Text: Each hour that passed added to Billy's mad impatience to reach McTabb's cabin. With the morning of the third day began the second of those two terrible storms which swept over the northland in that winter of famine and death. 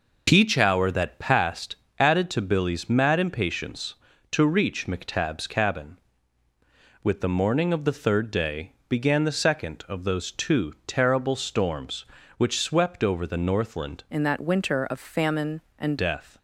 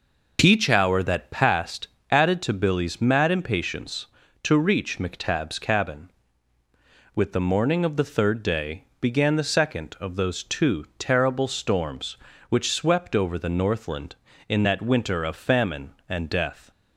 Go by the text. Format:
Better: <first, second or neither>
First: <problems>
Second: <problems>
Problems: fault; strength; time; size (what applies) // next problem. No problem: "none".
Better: second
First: pauses between "passed" and "added"; slight; at 1.7 s; 0.22 s long // pauses between "day" and "began"; slight; at 8.7 s; 0.18 s long // changes voice from "in" to "and"; from 14.0 to 15.9 s; 1.9 s long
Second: pauses between "passed" and "added"; slight; at 1.8 s; 0.22 s long // pauses between "day" and "began"; slight; at 8.8 s; 0.18 s long